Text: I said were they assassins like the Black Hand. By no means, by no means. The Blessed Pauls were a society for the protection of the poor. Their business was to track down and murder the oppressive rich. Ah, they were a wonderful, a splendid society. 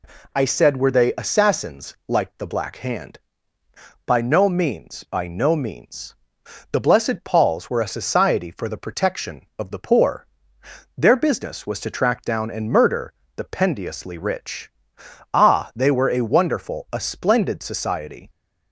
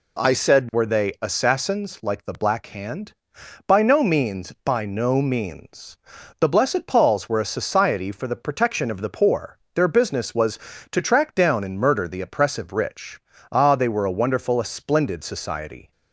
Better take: second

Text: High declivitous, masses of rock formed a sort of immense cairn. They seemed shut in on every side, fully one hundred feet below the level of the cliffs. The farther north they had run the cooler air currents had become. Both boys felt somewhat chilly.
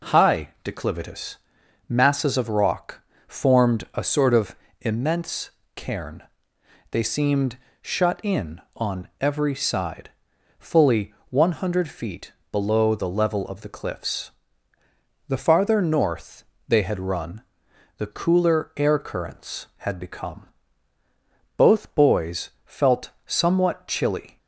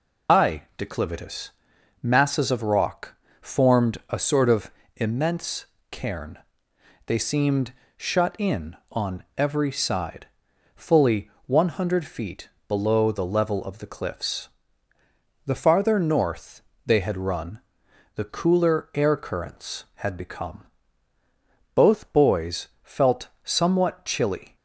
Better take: first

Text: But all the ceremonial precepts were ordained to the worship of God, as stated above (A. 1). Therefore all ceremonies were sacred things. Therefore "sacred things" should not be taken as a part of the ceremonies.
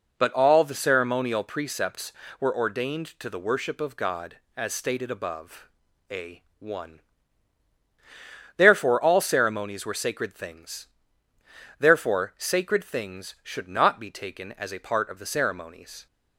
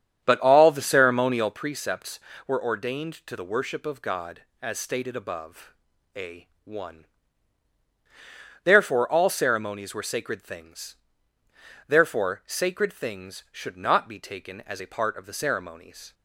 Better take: first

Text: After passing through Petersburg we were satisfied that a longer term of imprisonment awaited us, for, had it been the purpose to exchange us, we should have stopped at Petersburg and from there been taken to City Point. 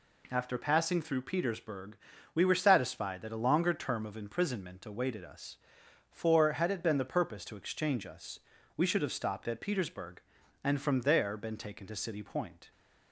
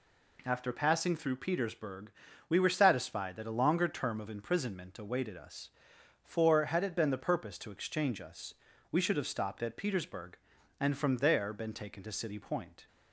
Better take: neither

